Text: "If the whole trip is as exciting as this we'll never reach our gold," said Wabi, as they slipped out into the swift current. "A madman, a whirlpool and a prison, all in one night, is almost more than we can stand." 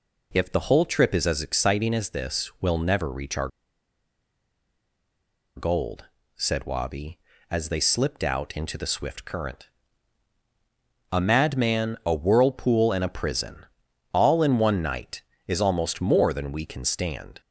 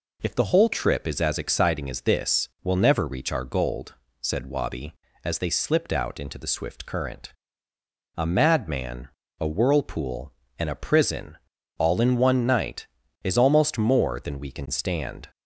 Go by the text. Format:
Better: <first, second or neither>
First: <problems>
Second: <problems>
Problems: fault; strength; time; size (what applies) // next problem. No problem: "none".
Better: second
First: pauses between "our" and "gold"; strong; at 3.5 s; 2.0 s long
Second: none